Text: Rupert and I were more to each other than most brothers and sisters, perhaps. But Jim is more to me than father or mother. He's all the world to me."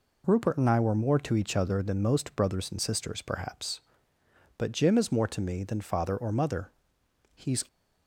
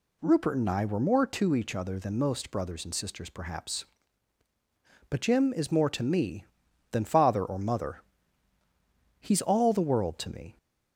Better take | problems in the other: second | stops before "all the world to me"; at 7.6 s

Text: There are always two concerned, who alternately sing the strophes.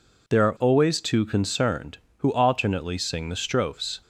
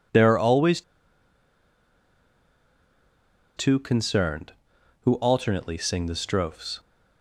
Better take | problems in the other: first | pauses between "always" and "two"; strong; at 0.8 s; 2.7 s long

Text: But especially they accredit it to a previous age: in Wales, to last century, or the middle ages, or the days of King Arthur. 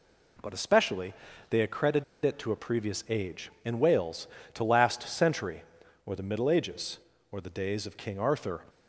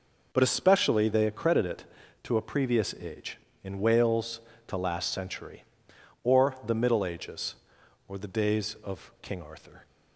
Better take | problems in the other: second | pauses between "especially" and "they"; slight; at 1.1 s; 0.36 s long // pauses between "accredit" and "it"; slight; at 2.0 s; 0.19 s long

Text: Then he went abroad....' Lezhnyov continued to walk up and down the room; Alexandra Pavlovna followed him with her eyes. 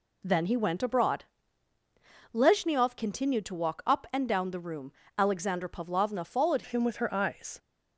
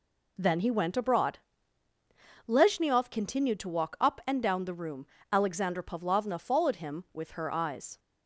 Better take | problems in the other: second | changes voice at "him"; from 6.6 s on; 0.9 s long

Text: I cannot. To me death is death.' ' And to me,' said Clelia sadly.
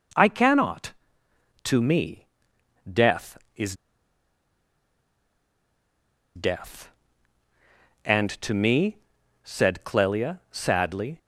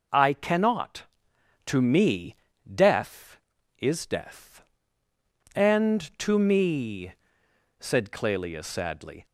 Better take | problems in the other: second | pauses between "me" and "death"; noticeable; at 2.2 s; 0.66 s long; also in the second // pauses between "is" and "death"; strong; at 3.7 s; 2.6 s long

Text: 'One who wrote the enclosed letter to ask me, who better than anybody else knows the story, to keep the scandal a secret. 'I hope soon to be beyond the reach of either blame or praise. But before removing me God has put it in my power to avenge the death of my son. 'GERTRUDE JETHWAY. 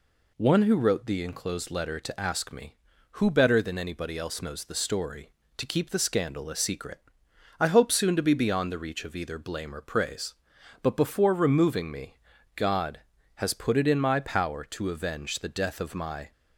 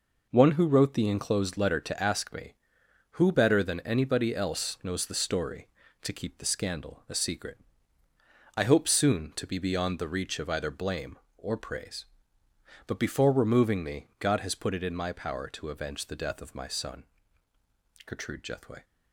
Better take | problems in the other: second | pauses between "me" and "God"; at 12.1 s; 0.38 s long // stops before "son GERTRUDE JETHWAY"; at 16.3 s

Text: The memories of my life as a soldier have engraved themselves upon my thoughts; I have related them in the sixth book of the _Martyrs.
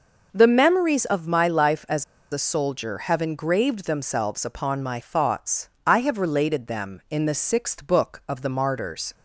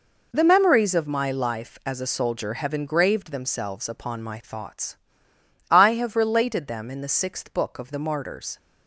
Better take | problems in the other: second | pauses between "as" and "a"; slight; at 2.0 s; 0.29 s long

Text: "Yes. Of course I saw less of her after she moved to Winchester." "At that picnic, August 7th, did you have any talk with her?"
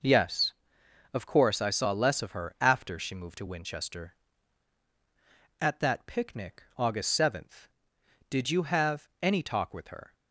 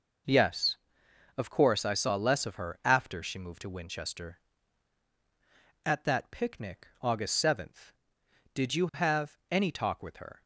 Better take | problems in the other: neither | none

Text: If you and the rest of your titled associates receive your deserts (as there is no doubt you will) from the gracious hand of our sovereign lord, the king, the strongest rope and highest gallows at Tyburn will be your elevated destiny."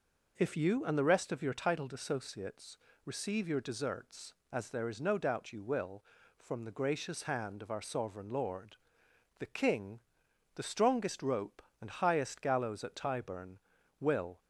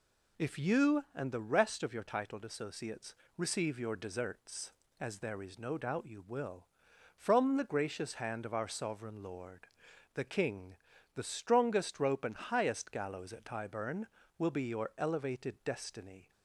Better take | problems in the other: second | pauses between "associates" and "receive"; slight; at 2.7 s; 0.28 s long; slight in the second // stops before "be your elevated destiny"; at 14.4 s

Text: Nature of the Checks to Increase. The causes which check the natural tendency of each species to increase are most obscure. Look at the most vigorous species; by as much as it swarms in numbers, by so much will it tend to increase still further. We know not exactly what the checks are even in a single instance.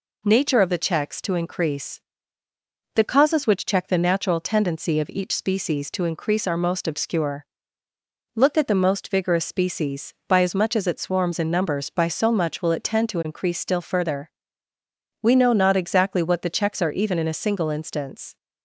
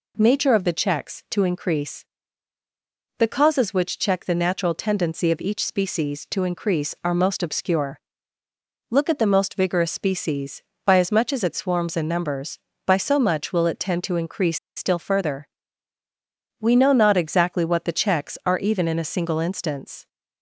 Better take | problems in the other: first | pauses between "increase" and "still"; slight; at 14.5 s; 0.18 s long

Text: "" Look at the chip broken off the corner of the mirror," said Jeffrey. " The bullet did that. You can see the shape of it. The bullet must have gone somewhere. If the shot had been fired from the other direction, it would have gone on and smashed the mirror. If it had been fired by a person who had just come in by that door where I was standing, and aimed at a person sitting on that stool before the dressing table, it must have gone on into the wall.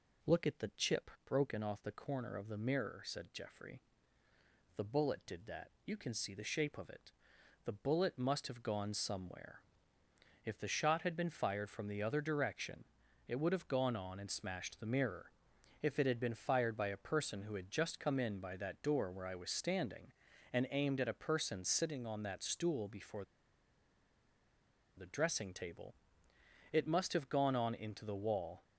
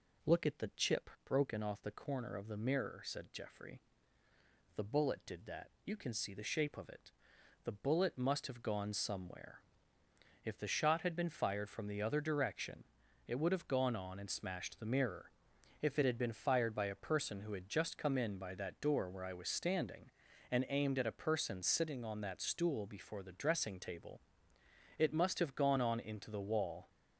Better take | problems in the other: second | pauses between "chip" and "broken"; slight; at 1.0 s; 0.16 s long; slight in the second // pauses between "before" and "the"; strong; at 23.2 s; 1.7 s long

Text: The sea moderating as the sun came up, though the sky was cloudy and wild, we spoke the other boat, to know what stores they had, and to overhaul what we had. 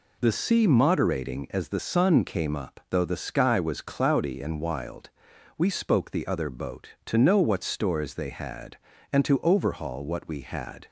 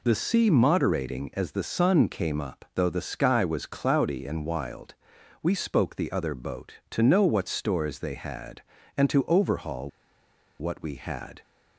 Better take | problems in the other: first | pauses between "overhaul" and "what"; noticeable; at 9.8 s; 0.71 s long

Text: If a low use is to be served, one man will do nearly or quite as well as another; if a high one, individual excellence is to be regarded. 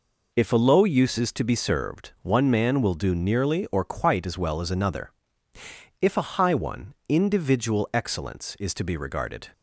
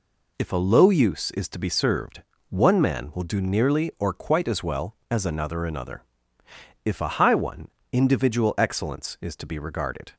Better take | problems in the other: first | says "another" twice; at 5.6 s

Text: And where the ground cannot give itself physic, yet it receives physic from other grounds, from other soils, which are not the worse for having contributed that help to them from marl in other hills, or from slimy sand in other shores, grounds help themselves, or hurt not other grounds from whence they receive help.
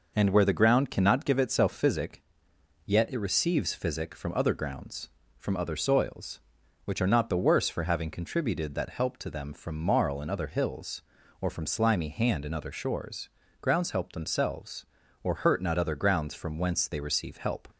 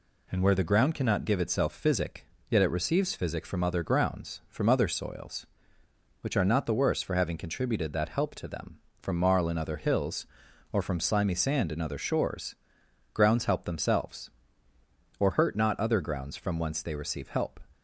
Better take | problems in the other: second | says "hand" for "sand"; at 12.0 s

